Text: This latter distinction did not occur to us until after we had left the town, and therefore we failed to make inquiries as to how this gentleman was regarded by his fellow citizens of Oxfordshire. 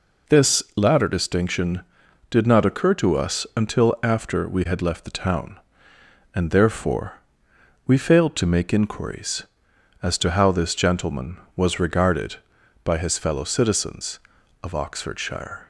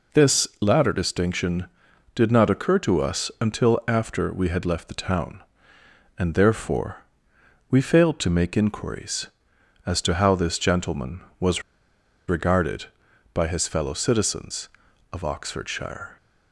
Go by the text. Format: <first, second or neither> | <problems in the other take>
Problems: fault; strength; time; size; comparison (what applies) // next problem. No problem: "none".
first | pauses between "therefore" and "we"; noticeable; at 7.0 s; 0.66 s long; noticeable in the first // pauses between "was" and "regarded"; noticeable; at 11.6 s; 0.66 s long